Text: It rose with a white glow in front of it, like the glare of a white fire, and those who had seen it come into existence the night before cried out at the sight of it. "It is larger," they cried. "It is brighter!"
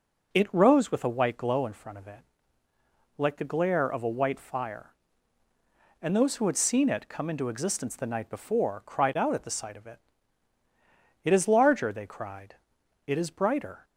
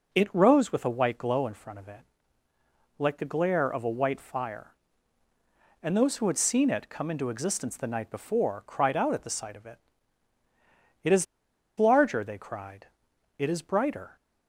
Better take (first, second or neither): first